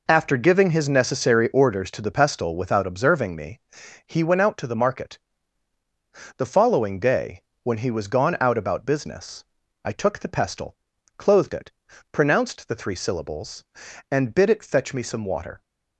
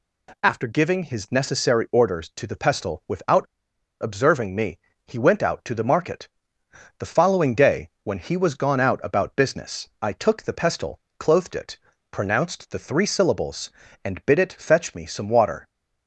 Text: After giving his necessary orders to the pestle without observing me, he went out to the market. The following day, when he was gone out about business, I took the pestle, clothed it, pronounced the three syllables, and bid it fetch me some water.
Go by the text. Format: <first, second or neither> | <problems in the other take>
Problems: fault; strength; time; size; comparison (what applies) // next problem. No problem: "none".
first | pauses between "without" and "observing"; noticeable; at 3.4 s; 0.57 s long